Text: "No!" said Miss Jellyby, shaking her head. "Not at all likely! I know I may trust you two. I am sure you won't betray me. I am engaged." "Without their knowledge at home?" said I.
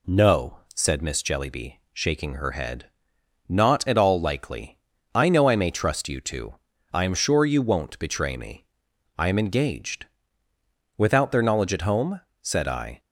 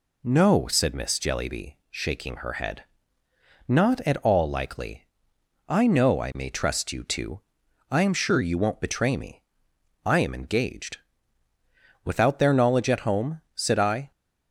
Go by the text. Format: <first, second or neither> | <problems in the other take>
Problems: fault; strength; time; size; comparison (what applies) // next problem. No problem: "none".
neither | none